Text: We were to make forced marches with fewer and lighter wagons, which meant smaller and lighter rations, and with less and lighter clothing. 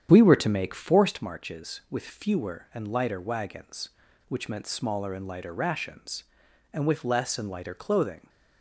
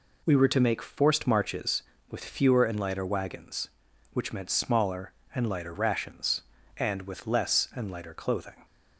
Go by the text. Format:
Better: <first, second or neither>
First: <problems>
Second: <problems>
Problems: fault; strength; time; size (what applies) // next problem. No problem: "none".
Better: second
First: starts louder than the rest; strong; until 1.2 s; 9 dB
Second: none